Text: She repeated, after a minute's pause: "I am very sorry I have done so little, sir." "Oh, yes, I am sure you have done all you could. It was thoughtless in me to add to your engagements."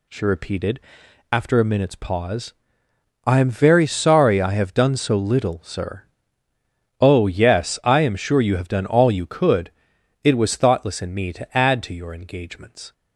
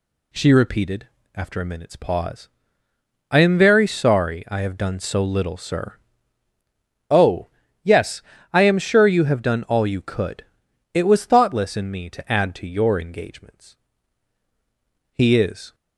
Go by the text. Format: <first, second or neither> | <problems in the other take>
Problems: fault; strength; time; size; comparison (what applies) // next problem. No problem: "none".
first | goes on to say "He is"; noticeable; from 15.1 s on; 0.62 s long